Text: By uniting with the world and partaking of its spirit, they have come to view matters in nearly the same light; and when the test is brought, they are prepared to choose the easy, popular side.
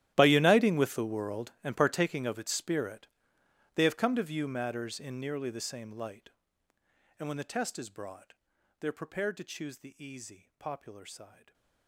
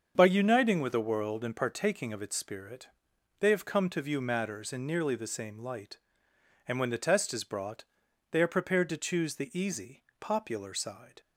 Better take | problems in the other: second | gets quieter; strong; throughout; 20 dB // starts louder than the rest; strong; until 1.1 s; 13 dB; also in the second // stays silent after the last word; slight; from 11.2 s on; 0.6 s long

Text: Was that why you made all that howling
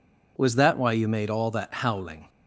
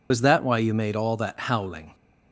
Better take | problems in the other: first | loses the start of "Was"; at 0.1 s; 85 ms

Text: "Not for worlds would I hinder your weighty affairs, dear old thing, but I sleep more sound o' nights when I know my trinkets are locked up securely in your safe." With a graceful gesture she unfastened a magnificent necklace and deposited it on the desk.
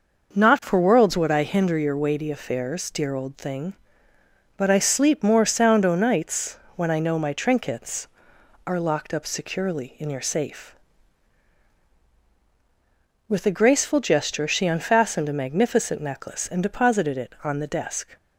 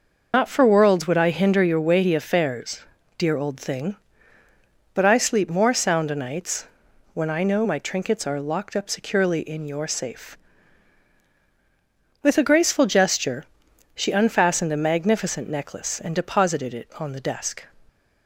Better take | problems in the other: first | loses the start of "Not"; at 0.3 s; 115 ms // pauses between "nights" and "when"; noticeable; at 6.6 s; 0.46 s long; slight in the first // pauses between "gesture" and "she"; noticeable; at 13.4 s; 0.48 s long

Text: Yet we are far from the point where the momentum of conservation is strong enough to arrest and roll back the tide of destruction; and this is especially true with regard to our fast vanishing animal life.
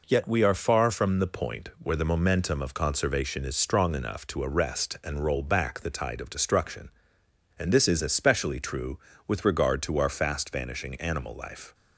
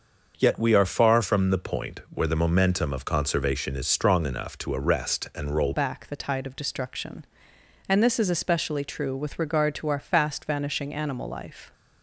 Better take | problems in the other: first | starts louder than the rest; until 1.3 s; 6.5 dB // changes voice at "back"; from 5.7 s on; 6.0 s long

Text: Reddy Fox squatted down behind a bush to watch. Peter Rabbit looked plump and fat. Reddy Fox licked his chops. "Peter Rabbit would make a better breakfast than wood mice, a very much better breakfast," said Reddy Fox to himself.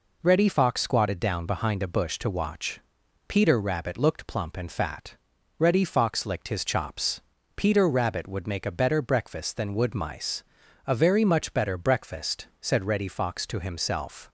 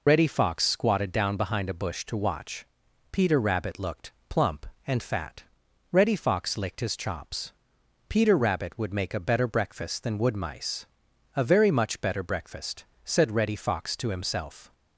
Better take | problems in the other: first | loses the start of "Reddy"; at 0.0 s; 70 ms // pauses between "looked" and "plump"; slight; at 4.1 s; 0.18 s long

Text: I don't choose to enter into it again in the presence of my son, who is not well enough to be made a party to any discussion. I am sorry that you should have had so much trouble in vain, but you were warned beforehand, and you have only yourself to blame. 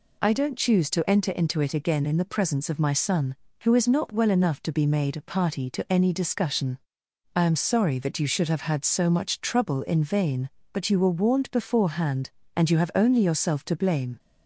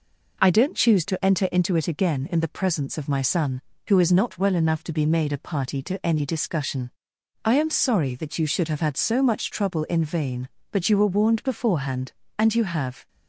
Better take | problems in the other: first | stops before "only yourself to blame"; at 13.0 s

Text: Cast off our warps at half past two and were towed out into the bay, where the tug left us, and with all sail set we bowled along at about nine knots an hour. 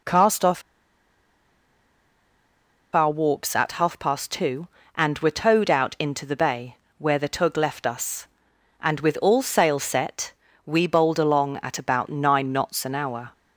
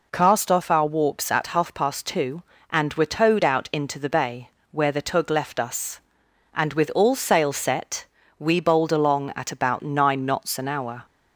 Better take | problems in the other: second | pauses between "off" and "our"; strong; at 0.6 s; 2.3 s long // pauses between "set" and "we"; slight; at 10.3 s; 0.32 s long; slight in the second

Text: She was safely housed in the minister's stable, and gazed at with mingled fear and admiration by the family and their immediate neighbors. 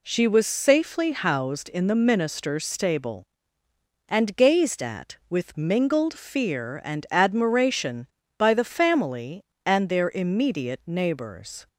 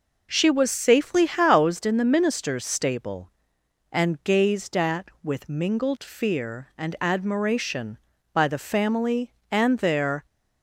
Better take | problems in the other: first | stops before "immediate neighbors"; at 10.2 s

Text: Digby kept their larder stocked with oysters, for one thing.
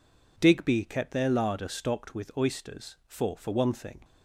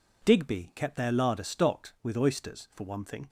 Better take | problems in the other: second | says "for" twice; at 3.3 s

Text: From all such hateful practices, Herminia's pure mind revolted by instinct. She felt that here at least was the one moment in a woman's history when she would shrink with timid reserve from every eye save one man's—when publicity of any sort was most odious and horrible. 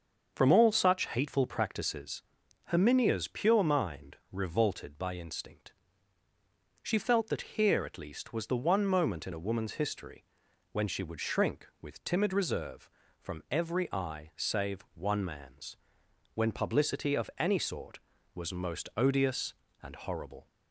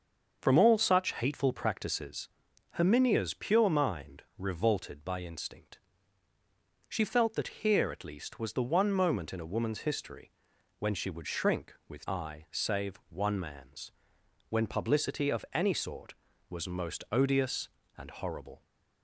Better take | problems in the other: first | starts louder than the rest; until 1.4 s; 6.5 dB; also in the first // pauses between "mind" and "revolted"; slight; at 4.2 s; 0.16 s long; slight in the first // pauses between "history" and "when"; noticeable; at 10.3 s; 0.46 s long; noticeable in the first // skips "timid reserve from every"; at 12.0 s

